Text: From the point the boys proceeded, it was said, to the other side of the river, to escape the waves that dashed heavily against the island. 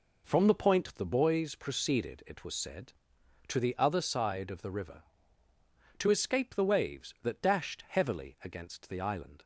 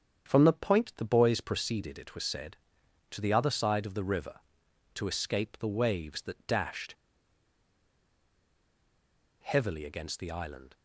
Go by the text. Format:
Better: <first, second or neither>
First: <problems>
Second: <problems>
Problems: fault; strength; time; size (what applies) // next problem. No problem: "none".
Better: first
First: none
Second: starts louder than the rest; strong; until 1.3 s; 8 dB // pauses between "dashed" and "heavily"; strong; at 6.9 s; 2.4 s long